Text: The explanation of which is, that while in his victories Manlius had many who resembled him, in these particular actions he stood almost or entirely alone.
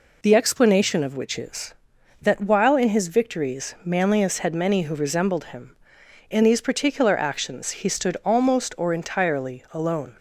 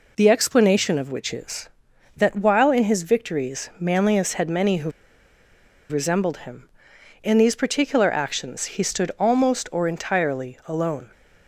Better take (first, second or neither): first